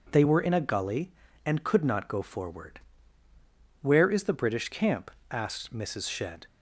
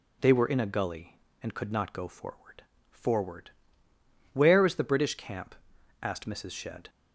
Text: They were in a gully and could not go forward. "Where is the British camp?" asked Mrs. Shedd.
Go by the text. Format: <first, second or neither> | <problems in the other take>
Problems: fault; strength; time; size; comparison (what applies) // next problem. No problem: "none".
first | says "forward" twice; at 2.8 s